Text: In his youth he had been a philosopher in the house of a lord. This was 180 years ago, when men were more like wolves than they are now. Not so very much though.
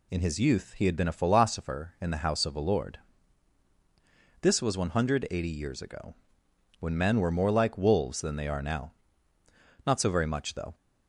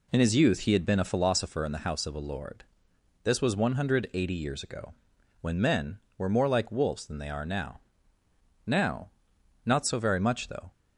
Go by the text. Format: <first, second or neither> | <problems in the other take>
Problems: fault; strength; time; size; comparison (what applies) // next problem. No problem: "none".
first | says "now" twice; at 8.6 s